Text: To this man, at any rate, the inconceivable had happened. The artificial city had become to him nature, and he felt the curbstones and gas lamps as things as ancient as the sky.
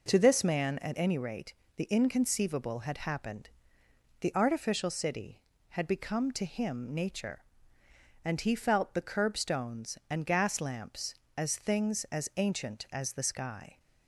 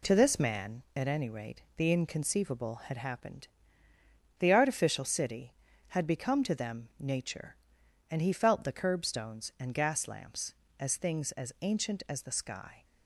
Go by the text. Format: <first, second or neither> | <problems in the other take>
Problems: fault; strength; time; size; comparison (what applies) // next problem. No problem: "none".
first | says "them" for "him"; at 6.5 s